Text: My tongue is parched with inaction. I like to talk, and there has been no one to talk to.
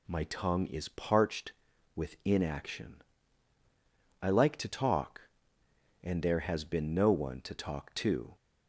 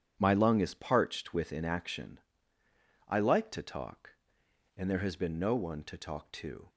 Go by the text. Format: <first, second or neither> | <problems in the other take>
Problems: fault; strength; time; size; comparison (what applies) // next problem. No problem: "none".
first | says "lung" for "tongue"; at 0.3 s